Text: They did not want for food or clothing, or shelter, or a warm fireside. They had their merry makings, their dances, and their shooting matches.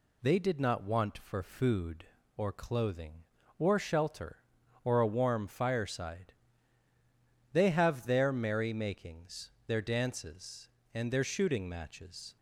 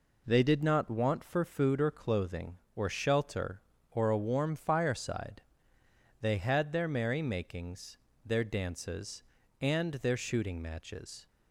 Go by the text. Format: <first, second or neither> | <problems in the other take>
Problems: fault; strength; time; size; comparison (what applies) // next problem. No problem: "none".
second | says "have" for "had"; at 7.7 s